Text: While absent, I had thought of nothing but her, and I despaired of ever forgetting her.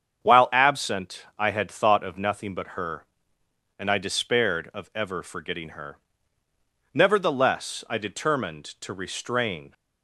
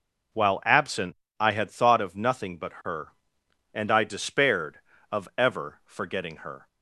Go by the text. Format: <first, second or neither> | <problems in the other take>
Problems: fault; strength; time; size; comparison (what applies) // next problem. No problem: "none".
second | starts louder than the rest; strong; until 1.3 s; 7.5 dB // goes on to say "Nevertheless I determined to restrain"; strong; from 6.9 s on; 2.8 s long